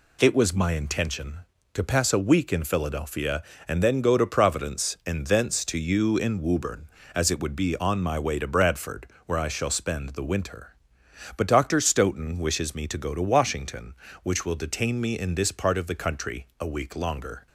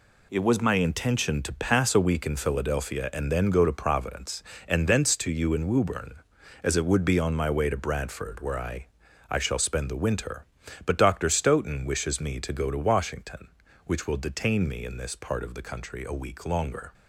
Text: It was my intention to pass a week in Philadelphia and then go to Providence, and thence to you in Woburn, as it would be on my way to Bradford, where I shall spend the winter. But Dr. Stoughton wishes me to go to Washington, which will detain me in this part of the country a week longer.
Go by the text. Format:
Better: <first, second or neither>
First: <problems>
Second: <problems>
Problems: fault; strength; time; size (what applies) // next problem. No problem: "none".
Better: first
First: none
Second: says "I" twice; at 9.2 s